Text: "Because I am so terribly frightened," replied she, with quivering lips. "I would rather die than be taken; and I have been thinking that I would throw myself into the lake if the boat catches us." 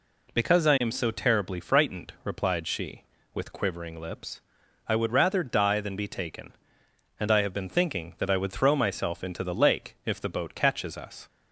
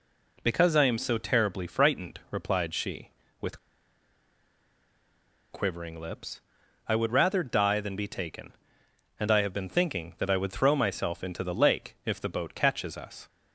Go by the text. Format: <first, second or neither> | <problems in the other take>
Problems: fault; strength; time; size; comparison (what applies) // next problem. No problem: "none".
first | pauses between "with" and "quivering"; strong; at 3.5 s; 1.9 s long